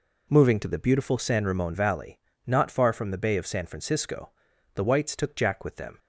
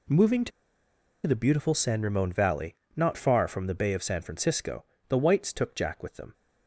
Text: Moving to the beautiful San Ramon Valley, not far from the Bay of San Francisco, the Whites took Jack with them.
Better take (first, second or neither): first